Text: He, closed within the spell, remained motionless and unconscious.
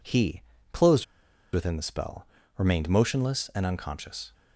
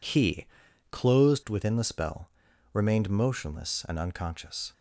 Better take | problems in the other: second | pauses between "closed" and "within"; noticeable; at 1.0 s; 0.48 s long

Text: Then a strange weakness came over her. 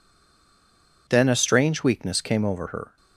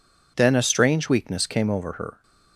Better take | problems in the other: second | stays silent before the first word; until 1.0 s; 1.0 s long

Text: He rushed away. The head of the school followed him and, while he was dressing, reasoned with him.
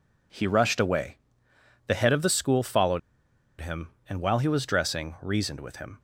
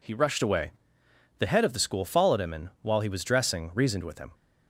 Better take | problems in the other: second | pauses between "followed" and "him"; noticeable; at 2.9 s; 0.61 s long

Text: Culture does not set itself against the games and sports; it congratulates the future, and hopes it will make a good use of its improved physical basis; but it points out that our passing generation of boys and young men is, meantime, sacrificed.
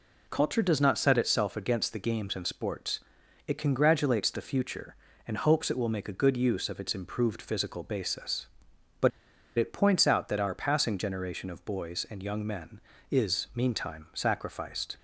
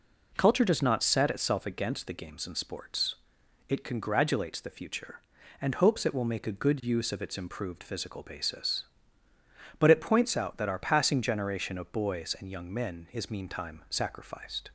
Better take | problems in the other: second | pauses between "but" and "it"; noticeable; at 9.1 s; 0.49 s long

